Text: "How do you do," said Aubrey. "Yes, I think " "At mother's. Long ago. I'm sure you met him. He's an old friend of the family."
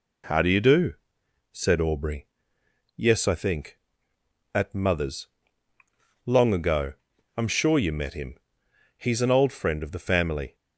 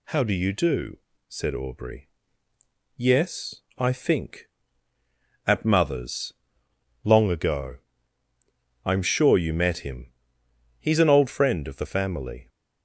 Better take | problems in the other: neither | none

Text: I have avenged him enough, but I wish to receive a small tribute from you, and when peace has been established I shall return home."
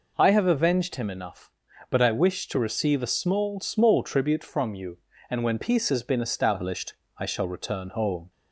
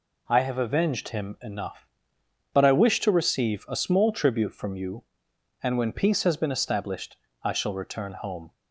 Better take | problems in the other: second | says "small" twice; at 3.5 s // pauses between "established" and "I"; slight; at 6.9 s; 0.24 s long; slight in the second

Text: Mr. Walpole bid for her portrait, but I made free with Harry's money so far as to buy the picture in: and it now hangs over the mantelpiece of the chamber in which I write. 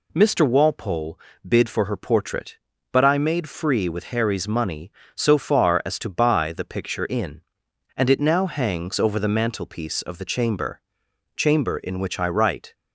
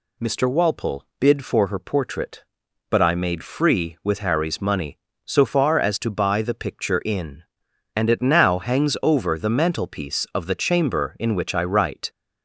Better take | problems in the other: second | pauses between "Walpole" and "bid"; slight; at 1.1 s; 0.28 s long; slight in the second // says "chamber" twice; at 11.3 s

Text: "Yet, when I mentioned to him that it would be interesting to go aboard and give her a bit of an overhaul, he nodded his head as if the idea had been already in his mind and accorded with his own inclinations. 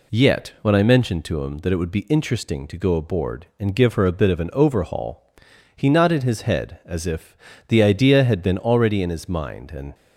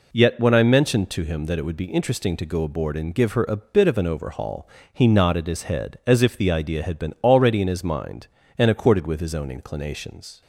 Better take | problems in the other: second | pauses between "if" and "the"; slight; at 7.3 s; 0.30 s long // stops before "accorded with his own inclinations"; at 9.9 s

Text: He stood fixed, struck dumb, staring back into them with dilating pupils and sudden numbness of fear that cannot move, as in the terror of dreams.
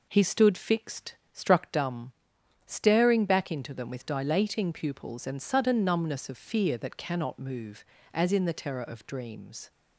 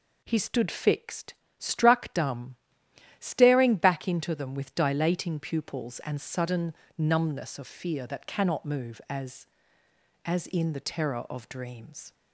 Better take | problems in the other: first | pauses between "sudden" and "numbness"; slight; at 6.7 s; 0.24 s long // says "as" twice; at 10.2 s

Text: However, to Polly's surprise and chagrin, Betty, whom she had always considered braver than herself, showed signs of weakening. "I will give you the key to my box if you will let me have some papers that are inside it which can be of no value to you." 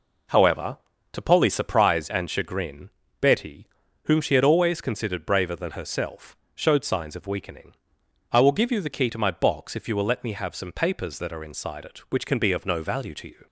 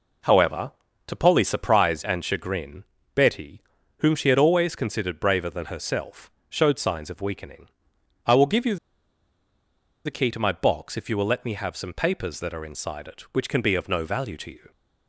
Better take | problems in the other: first | pauses between "you" and "the"; strong; at 8.7 s; 1.2 s long

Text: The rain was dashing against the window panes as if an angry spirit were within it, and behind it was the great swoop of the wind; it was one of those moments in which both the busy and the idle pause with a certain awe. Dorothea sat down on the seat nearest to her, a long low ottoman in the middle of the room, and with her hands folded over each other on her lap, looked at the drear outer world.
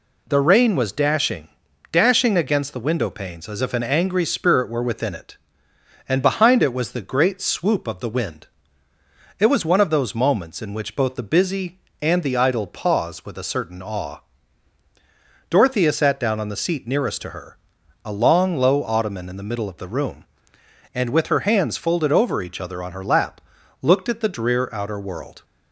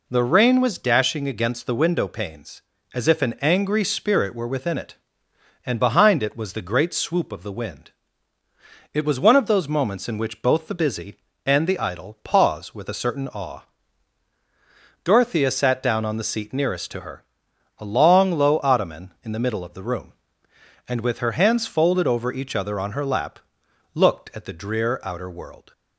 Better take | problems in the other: second | says "dashing" twice; at 1.9 s

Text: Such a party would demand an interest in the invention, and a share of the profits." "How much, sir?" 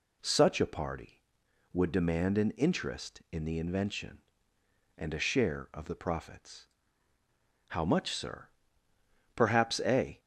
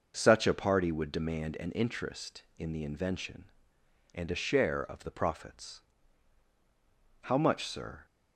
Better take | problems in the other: second | goes on to say "Perhaps a"; noticeable; from 9.3 s on; 0.82 s long

